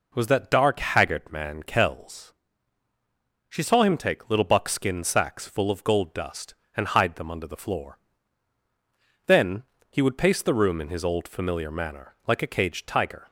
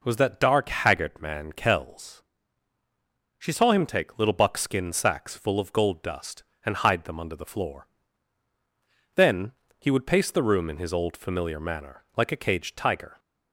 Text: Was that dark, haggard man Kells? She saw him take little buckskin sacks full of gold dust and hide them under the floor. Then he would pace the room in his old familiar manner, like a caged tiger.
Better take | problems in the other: neither | pauses between "Then" and "he"; slight; the same in both

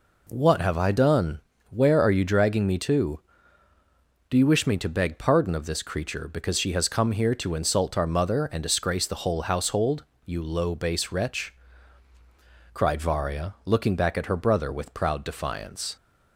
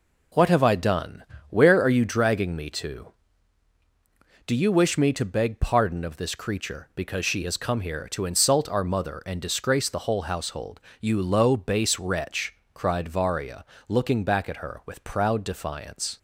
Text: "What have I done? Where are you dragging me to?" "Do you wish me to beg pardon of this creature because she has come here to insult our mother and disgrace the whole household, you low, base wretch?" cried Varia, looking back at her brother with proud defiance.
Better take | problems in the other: first | skips "brother"; at 14.8 s

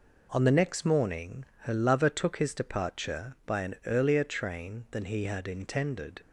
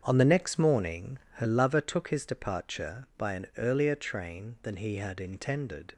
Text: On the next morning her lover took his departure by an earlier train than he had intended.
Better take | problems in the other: first | starts louder than the rest; strong; until 1.7 s; 7.5 dB // pauses between "morning" and "her"; slight; at 1.1 s; 0.18 s long; slight in the first

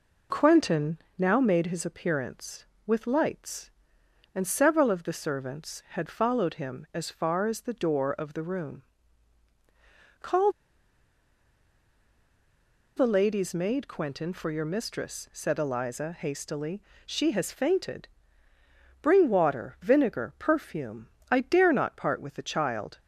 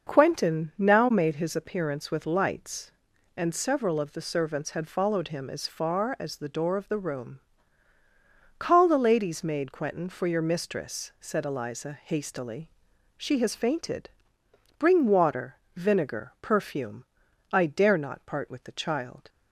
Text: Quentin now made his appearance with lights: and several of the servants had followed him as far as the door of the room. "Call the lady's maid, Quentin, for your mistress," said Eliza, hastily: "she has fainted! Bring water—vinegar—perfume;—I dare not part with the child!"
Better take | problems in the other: second | pauses between "Quentin" and "now"; slight; at 0.9 s; 0.20 s long // pauses between "Call" and "the"; strong; at 10.5 s; 2.4 s long

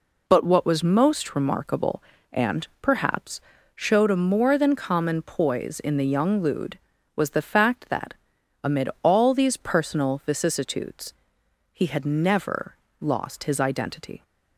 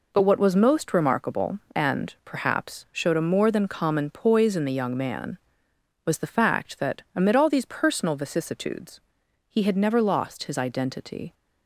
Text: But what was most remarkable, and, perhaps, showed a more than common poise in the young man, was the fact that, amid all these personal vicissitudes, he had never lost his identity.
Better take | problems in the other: second | says "lude" for "man"; at 6.4 s // pauses between "never" and "lost"; slight; at 12.7 s; 0.26 s long

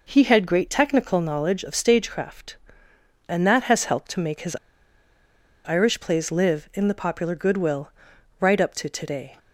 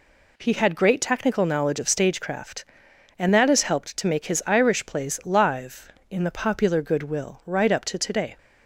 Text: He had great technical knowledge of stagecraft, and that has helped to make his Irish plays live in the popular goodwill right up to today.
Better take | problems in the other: second | pauses between "his" and "Irish"; at 4.5 s; 1.1 s long // pauses between "goodwill" and "right"; noticeable; at 7.9 s; 0.48 s long

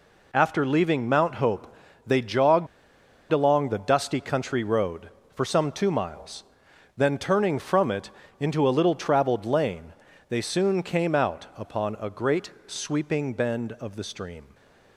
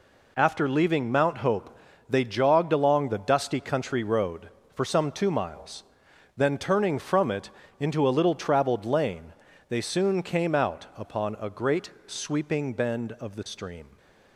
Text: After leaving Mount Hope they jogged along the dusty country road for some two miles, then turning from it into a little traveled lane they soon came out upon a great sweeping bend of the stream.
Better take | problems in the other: second | pauses between "Hope" and "they"; slight; at 1.7 s; 0.32 s long; slight in the second // pauses between "jogged" and "along"; noticeable; at 2.6 s; 0.65 s long // pauses between "it" and "into"; slight; at 8.1 s; 0.30 s long; slight in the second // pauses between "lane" and "they"; slight; at 9.9 s; 0.36 s long; slight in the second // pauses between "great" and "sweeping"; slight; at 12.5 s; 0.16 s long; slight in the second // stays silent after the last word; slight; from 14.4 s on; 0.5 s long

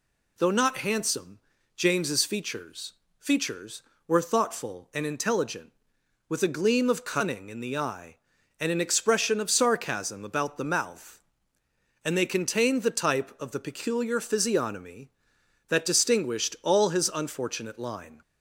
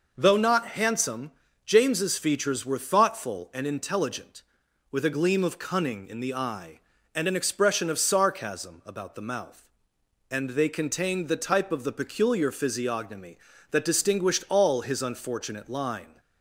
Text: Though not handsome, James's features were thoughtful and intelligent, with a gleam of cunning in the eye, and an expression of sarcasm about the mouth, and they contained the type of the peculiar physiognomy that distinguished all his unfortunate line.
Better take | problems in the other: second | says "features" twice; at 3.1 s

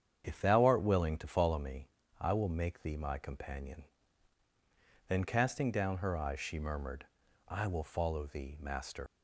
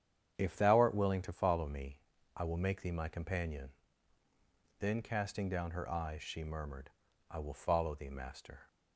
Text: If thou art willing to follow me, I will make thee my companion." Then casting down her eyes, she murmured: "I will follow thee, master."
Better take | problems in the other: second | starts louder than the rest; strong; until 1.2 s; 8 dB; strong in the second // leaves "master" unfinished; at 9.0 s; 110 ms

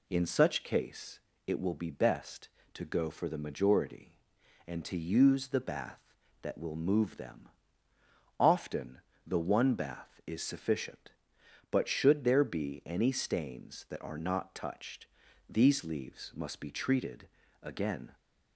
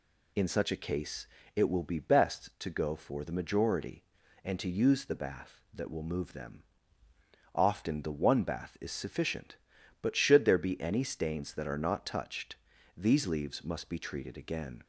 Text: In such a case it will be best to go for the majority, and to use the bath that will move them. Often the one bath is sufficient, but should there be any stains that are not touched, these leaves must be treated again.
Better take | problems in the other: second | skips "a"; at 0.6 s // pauses between "case" and "it"; slight; at 1.1 s; 0.28 s long; slight in the second // pauses between "Often" and "the"; slight; at 8.9 s; 0.28 s long // pauses between "treated" and "again"; slight; at 17.2 s; 0.36 s long

